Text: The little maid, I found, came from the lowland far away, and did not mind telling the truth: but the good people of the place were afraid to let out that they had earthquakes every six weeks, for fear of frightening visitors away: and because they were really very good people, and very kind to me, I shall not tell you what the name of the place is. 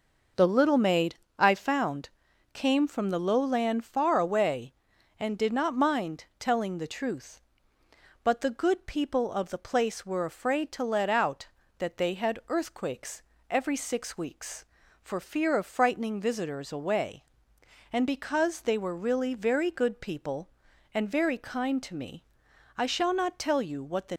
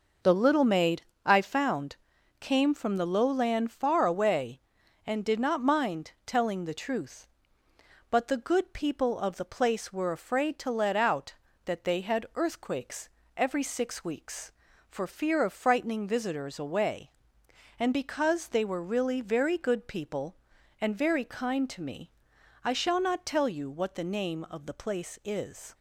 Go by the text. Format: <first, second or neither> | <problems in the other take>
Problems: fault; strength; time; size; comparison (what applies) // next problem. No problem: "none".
second | pauses between "earthquakes" and "every"; slight; at 13.2 s; 0.28 s long; slight in the second // stops before "name of the place is"; at 24.1 s